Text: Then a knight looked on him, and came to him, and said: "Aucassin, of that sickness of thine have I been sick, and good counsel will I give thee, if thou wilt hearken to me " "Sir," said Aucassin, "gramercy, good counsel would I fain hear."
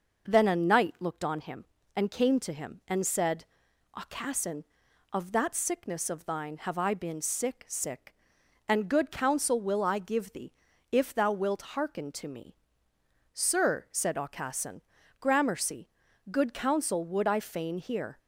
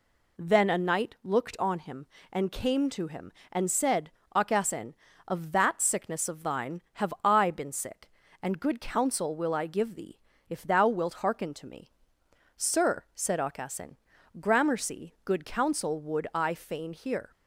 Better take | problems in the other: second | says "sick" twice; at 7.6 s

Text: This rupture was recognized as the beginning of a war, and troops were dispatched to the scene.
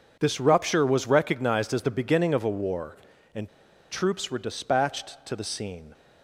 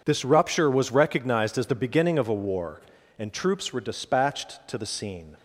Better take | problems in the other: second | pauses between "and" and "troops"; at 3.4 s; 0.42 s long

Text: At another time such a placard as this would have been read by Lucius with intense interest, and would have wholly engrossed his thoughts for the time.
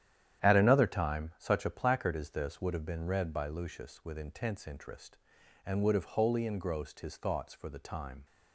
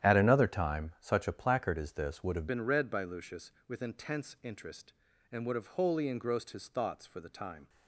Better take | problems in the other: first | starts louder than the rest; strong; until 1.1 s; 10.5 dB; strong in the first // changes voice at "been"; from 2.4 s on; 5.2 s long

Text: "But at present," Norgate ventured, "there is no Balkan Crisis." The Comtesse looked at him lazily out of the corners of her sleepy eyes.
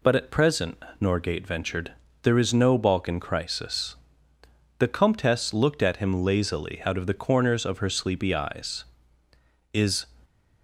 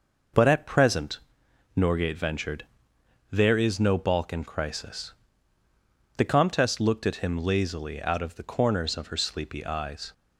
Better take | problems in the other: second | goes on to say "Is"; slight; from 9.7 s on; 0.34 s long

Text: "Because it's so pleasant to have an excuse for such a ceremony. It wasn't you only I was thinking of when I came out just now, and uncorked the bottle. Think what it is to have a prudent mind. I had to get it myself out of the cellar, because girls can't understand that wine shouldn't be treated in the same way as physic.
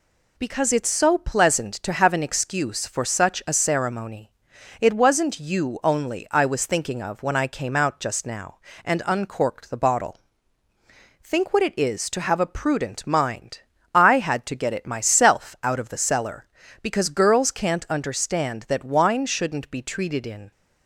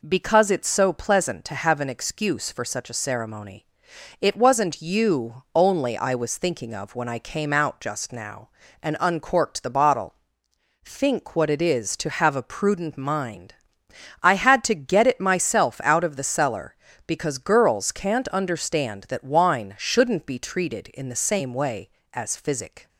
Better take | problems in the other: second | stops before "the same way as physic"; at 20.5 s

